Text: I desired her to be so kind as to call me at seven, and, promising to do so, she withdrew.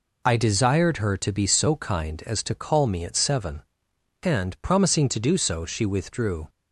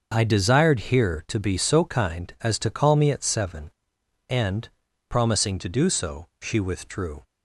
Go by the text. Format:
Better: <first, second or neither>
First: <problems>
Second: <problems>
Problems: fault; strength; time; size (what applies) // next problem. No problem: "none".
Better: first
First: none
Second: starts louder than the rest; noticeable; until 1.1 s; 6 dB // says "here" for "her"; at 0.9 s